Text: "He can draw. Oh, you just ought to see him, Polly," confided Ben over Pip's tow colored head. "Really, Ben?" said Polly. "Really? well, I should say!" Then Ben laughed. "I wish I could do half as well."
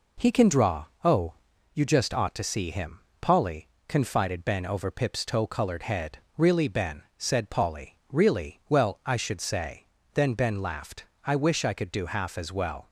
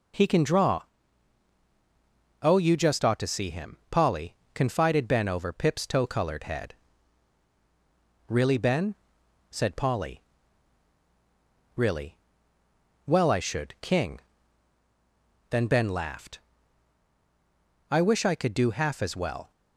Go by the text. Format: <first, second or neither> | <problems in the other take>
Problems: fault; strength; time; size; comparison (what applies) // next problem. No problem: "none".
first | says "king" for "say"; at 13.8 s